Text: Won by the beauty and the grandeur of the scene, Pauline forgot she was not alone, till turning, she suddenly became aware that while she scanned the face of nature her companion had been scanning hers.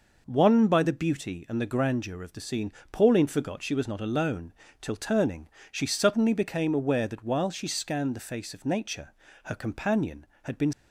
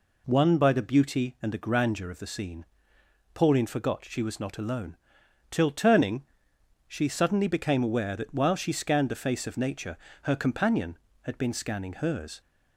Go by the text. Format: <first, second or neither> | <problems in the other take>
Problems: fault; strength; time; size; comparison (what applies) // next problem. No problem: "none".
second | pauses between "nature" and "her"; slight; at 9.1 s; 0.32 s long; slight in the second // stops before "scanning hers"; at 10.7 s